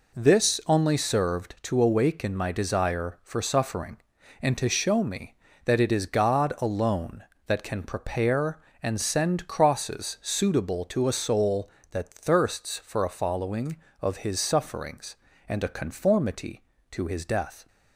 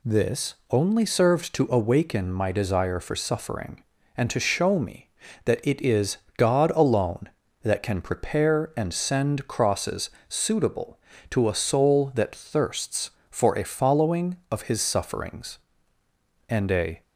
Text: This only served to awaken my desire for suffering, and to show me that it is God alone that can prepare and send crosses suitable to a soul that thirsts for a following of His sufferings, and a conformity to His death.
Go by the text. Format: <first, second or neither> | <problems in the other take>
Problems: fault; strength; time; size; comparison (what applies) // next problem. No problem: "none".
first | pauses between "This" and "only"; slight; at 0.5 s; 0.16 s long // pauses between "is" and "God"; slight; at 6.1 s; 0.20 s long // pauses between "crosses" and "suitable"; slight; at 10.0 s; 0.18 s long // stops before "conformity to His death"; at 17.0 s